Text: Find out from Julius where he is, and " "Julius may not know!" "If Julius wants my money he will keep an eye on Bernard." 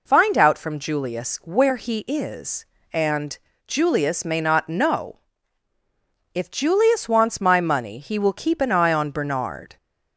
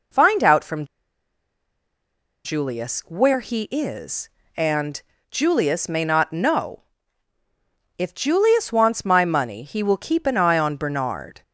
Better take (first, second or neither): first